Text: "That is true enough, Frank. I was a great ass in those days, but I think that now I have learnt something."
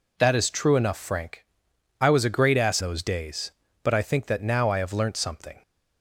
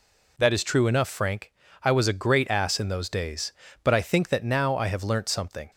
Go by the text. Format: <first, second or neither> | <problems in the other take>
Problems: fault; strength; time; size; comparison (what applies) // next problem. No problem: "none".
second | skips "in"; at 2.8 s